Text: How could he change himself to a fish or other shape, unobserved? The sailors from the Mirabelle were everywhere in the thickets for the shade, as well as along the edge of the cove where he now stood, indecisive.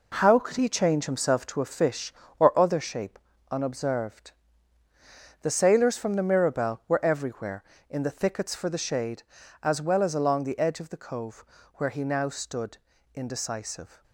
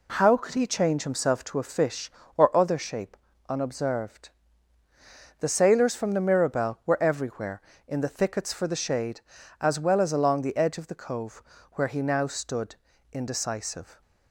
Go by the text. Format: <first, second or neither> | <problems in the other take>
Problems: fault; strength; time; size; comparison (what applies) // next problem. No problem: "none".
second | gets quieter; strong; throughout; 7.5 dB // pauses between "cove" and "where"; slight; at 11.4 s; 0.34 s long; slight in the second